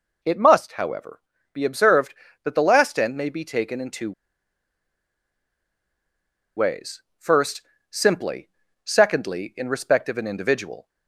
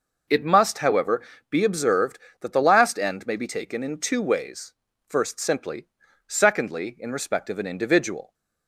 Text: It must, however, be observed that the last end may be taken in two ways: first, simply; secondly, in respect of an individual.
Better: second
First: pauses between "two" and "ways"; strong; at 4.1 s; 2.4 s long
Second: none

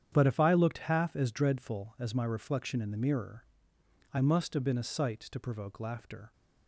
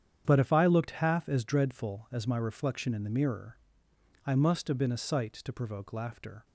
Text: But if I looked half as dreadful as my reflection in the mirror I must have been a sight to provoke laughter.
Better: neither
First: starts louder than the rest; strong; until 1.1 s; 9 dB // pauses between "mirror" and "I"; noticeable; at 3.4 s; 0.70 s long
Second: starts louder than the rest; strong; until 1.2 s; 9 dB // pauses between "mirror" and "I"; noticeable; at 3.5 s; 0.70 s long

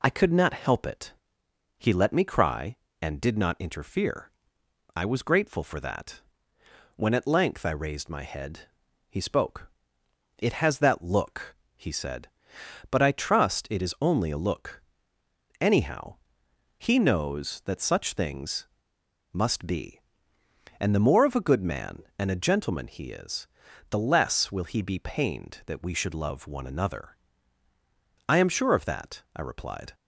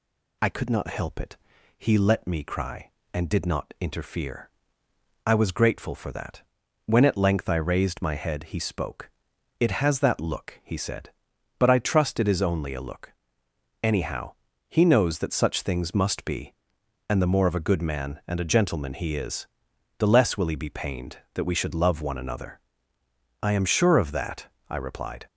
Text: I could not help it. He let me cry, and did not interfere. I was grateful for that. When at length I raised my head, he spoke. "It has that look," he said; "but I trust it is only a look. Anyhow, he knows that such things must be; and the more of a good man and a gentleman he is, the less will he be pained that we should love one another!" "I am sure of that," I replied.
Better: second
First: pauses between "things" and "must"; noticeable; at 18.6 s; 0.65 s long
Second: none

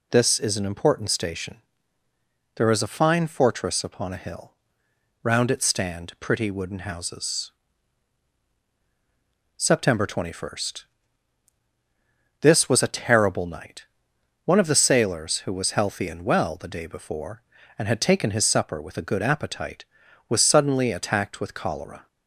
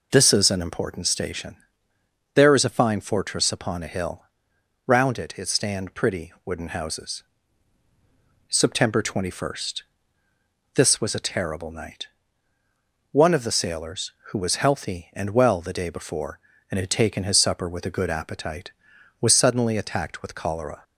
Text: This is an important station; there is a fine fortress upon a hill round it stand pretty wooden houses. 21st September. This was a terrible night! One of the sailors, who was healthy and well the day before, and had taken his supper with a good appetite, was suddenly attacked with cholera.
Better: first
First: pauses between "hill" and "round"; noticeable; at 4.5 s; 0.68 s long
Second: pauses between "hill" and "round"; noticeable; at 4.2 s; 0.64 s long // says "it" twice; at 5.3 s

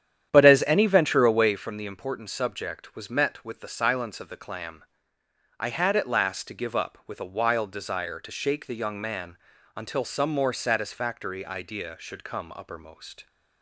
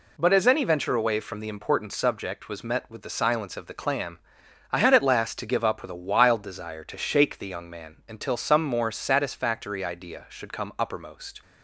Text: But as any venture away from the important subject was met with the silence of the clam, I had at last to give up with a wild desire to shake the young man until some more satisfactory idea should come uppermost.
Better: second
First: starts louder than the rest; strong; until 1.7 s; 9.5 dB // pauses between "man" and "until"; at 9.3 s; 0.38 s long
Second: none

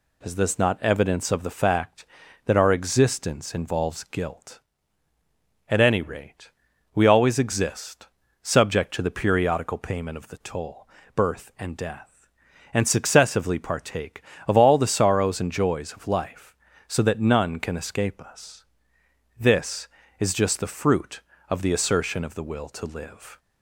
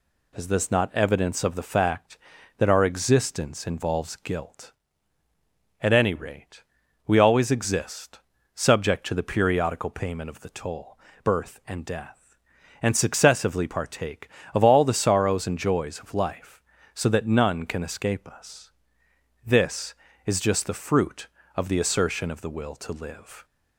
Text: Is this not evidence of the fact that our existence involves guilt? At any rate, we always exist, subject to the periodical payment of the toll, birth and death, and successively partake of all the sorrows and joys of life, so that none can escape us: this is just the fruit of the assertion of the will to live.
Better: neither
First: none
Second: none

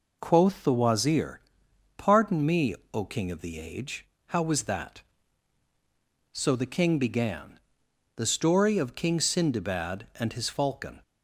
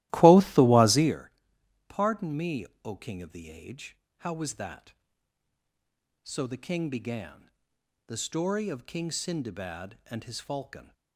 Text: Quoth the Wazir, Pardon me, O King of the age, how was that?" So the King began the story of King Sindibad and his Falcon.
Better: first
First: pauses between "began" and "the"; noticeable; at 7.5 s; 0.56 s long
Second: starts louder than the rest; strong; until 1.2 s; 16.5 dB // pauses between "began" and "the"; noticeable; at 7.4 s; 0.56 s long

